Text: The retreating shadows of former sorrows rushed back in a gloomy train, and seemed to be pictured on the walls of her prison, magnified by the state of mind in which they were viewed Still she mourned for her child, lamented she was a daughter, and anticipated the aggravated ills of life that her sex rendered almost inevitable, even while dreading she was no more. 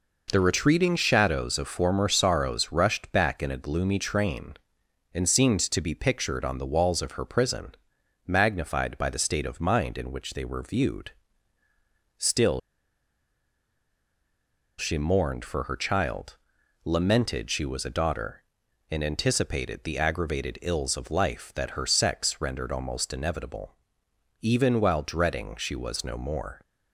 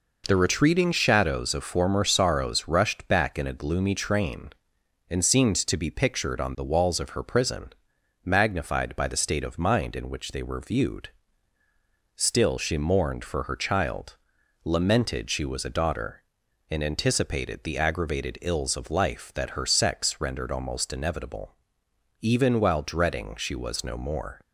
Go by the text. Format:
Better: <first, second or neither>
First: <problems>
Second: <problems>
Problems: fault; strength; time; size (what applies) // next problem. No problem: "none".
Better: second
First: pauses between "viewed" and "Still"; at 11.1 s; 1.0 s long // pauses between "Still" and "she"; strong; at 12.5 s; 2.1 s long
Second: pauses between "viewed" and "Still"; at 11.0 s; 1.0 s long